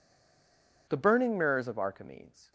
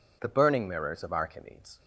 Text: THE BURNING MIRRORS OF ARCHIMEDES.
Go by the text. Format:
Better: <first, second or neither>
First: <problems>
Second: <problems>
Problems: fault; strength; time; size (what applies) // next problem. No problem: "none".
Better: second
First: stays silent before the first word; slight; until 0.8 s; 0.8 s long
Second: none